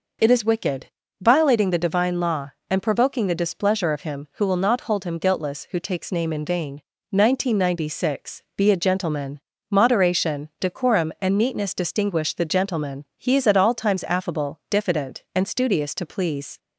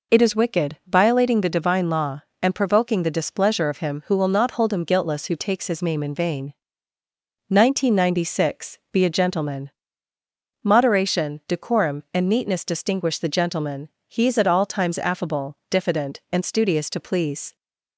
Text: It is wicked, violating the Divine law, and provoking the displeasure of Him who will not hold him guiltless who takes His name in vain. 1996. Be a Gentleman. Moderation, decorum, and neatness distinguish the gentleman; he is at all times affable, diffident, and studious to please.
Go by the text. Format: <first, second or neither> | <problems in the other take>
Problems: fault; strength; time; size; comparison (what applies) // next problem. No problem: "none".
second | skips "His"; at 6.1 s